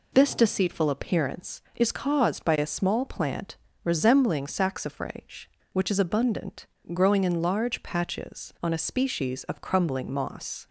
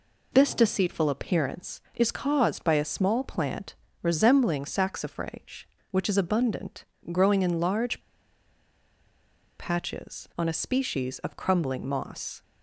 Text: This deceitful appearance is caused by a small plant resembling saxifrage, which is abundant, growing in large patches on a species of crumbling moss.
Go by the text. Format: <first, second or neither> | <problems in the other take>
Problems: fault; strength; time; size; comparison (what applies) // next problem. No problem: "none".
first | pauses between "plant" and "resembling"; slight; at 3.7 s; 0.26 s long; slight in the first // pauses between "large" and "patches"; strong; at 8.0 s; 1.5 s long